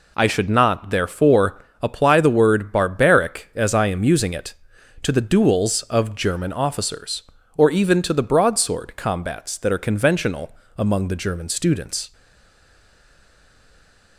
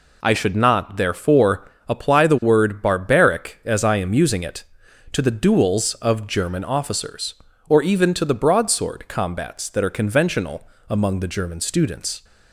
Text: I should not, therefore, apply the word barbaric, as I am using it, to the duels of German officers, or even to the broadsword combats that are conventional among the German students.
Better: second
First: pauses between "conventional" and "among"; slight; at 10.5 s; 0.22 s long // stays silent after the last word; from 12.1 s on; 2.0 s long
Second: pauses between "conventional" and "among"; slight; at 10.6 s; 0.22 s long

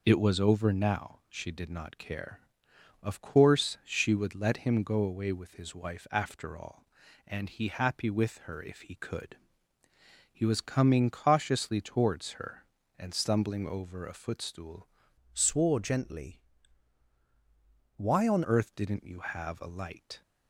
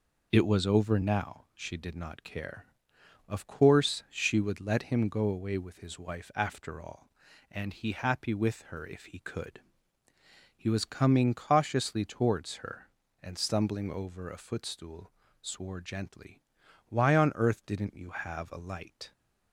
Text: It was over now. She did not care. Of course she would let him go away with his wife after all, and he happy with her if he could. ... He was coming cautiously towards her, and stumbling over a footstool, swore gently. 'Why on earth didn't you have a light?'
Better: second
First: changes voice from "swore" to "on"; from 15.3 to 18.4 s; 3.1 s long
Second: none

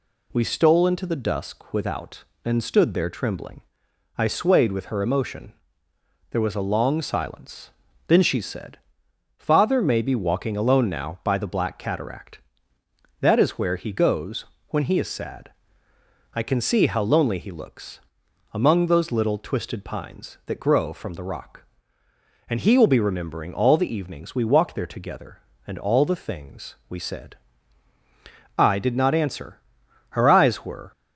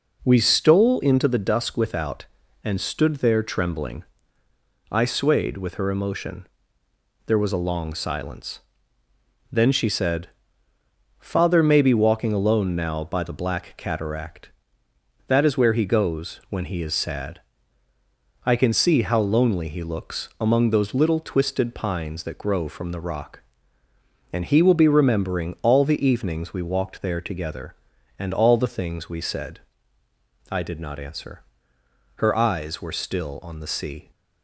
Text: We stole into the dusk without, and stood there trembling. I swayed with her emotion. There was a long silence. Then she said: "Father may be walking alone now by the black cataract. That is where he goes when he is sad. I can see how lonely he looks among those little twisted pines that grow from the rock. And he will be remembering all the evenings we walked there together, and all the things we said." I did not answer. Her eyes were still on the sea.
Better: second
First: pauses between "goes" and "when"; slight; at 14.4 s; 0.24 s long // pauses between "looks" and "among"; noticeable; at 17.9 s; 0.54 s long // stops before "still on the sea"; at 30.9 s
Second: none

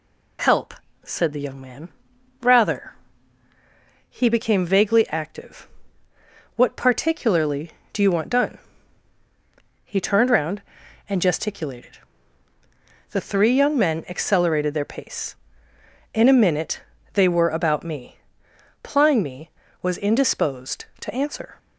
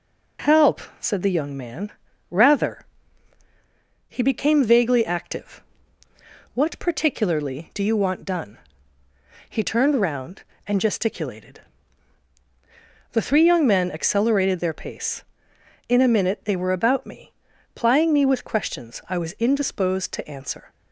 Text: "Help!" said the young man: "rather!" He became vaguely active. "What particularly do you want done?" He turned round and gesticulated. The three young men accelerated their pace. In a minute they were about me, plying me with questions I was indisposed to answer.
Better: second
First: pauses between "minute" and "they"; slight; at 16.8 s; 0.32 s long // skips "with questions I"; at 19.6 s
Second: none

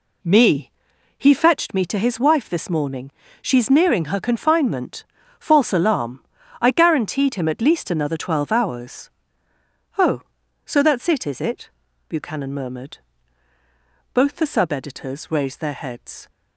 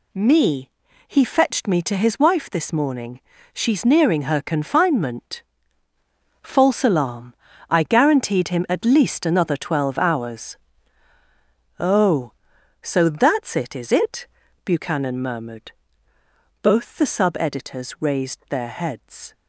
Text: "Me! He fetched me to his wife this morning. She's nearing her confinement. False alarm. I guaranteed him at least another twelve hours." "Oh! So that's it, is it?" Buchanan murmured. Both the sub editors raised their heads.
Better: second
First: starts louder than the rest; slight; until 1.7 s; 2.5 dB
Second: none

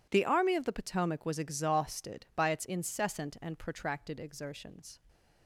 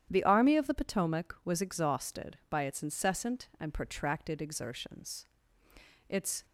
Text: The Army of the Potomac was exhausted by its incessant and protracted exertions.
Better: first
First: none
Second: starts louder than the rest; strong; until 1.1 s; 10 dB // goes on to say "Its"; slight; from 6.0 s on; 0.36 s long

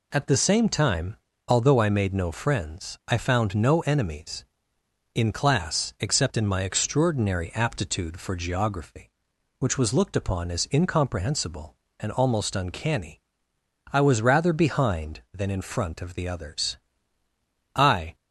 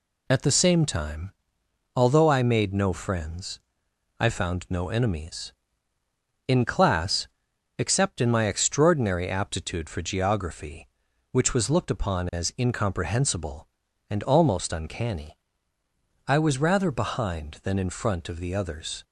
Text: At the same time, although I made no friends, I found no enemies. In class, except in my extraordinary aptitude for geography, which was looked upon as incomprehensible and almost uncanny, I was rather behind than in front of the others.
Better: second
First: goes on to say "I"; slight; from 17.7 s on; 0.40 s long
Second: none

